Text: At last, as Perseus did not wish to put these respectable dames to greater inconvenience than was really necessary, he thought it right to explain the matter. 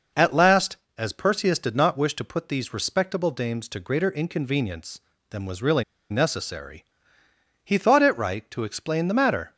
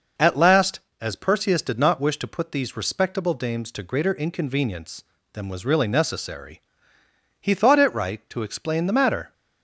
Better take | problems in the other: second | pauses between "really" and "necessary"; slight; at 5.8 s; 0.28 s long

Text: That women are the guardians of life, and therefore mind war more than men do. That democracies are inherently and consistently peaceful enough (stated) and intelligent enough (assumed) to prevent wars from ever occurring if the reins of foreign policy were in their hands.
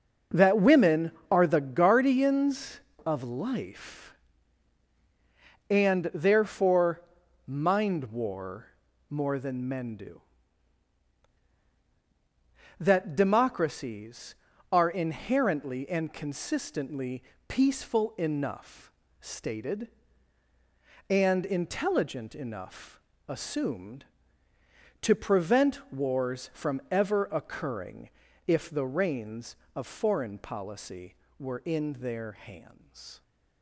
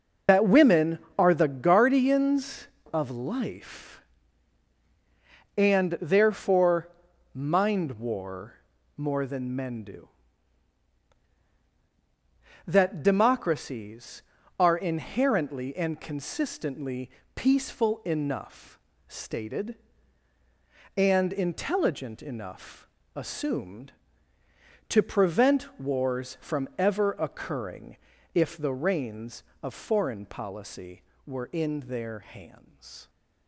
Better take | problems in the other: first | loses the start of "That"; at 0.2 s; 105 ms // pauses between "therefore" and "mind"; at 6.8 s; 0.44 s long; also in the first // pauses between "war" and "more"; at 8.5 s; 0.42 s long; also in the first // pauses between "consistently" and "peaceful"; slight; at 17.0 s; 0.24 s long; slight in the first // pauses between "occurring" and "if"; slight; at 27.9 s; 0.36 s long; slight in the first

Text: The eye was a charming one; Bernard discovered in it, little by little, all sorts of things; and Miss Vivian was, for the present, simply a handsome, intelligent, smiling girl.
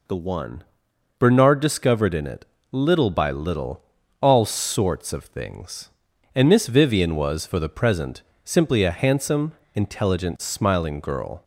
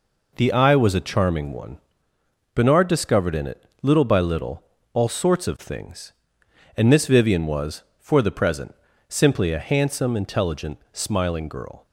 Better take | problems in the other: second | skips "eye was a charming"; at 0.1 s

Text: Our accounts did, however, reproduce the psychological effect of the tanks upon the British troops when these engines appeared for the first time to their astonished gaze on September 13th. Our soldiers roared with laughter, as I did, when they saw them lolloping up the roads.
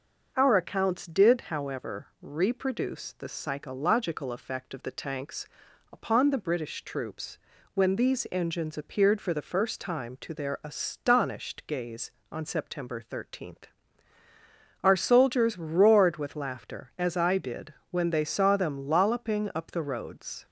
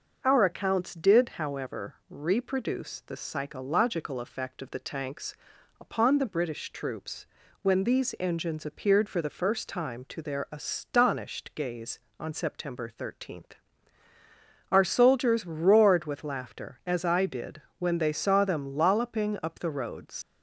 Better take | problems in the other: first | starts louder than the rest; noticeable; until 1.2 s; 6 dB; noticeable in the first // pauses between "tanks" and "upon"; noticeable; at 5.3 s; 0.46 s long; noticeable in the first // pauses between "troops" and "when"; slight; at 7.2 s; 0.36 s long; slight in the first // leaves "roads" unfinished; at 20.2 s; 110 ms

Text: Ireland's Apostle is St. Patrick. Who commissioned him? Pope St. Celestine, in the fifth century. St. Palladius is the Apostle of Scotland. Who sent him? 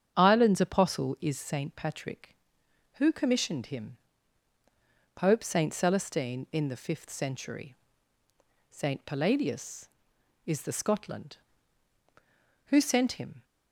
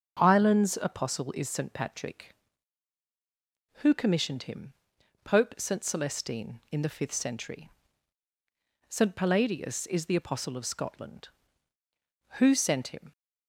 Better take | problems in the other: second | starts louder than the rest; strong; until 1.1 s; 8 dB; noticeable in the second // skips "Apostle of"; at 10.7 s

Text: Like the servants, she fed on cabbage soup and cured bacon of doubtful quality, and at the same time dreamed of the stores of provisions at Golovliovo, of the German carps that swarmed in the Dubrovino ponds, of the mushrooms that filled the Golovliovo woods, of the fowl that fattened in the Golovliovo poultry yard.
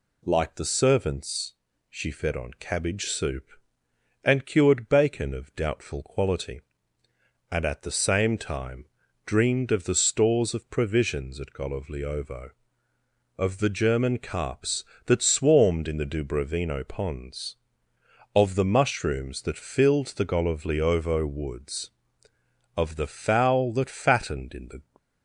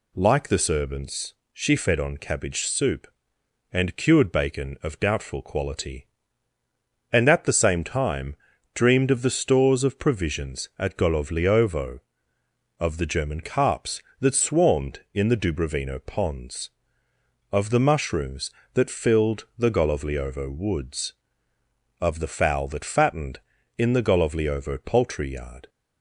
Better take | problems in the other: second | pauses between "time" and "dreamed"; at 8.8 s; 0.40 s long; also in the second // stops before "Golovliovo poultry yard"; at 24.9 s

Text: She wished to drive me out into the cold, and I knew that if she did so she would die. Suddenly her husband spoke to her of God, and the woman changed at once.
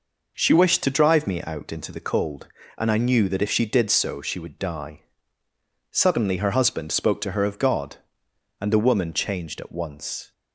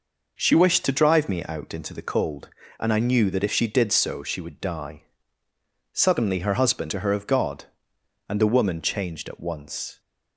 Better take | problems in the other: first | skips "spoke"; at 6.8 s

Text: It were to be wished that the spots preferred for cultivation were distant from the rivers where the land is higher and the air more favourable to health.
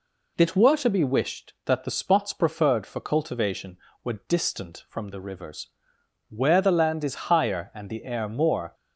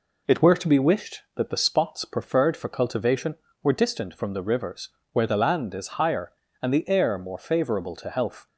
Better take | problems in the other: second | pauses between "rivers" and "where"; noticeable; at 5.6 s; 0.60 s long; slight in the second // stops before "favourable to health"; at 8.7 s

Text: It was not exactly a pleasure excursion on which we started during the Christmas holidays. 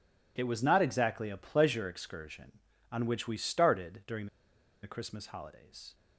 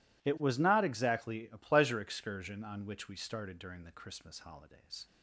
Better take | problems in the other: second | pauses between "during" and "the"; noticeable; at 4.2 s; 0.56 s long

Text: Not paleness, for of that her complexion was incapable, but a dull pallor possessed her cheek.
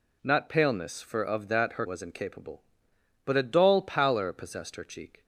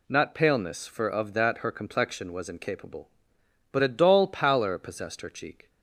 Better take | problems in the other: second | skips "complexion"; at 1.8 s

